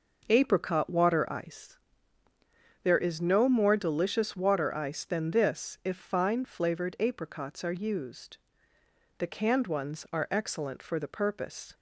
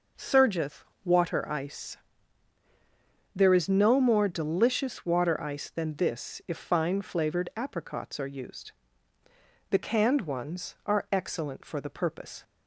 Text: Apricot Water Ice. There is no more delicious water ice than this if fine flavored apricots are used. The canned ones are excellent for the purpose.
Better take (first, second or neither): first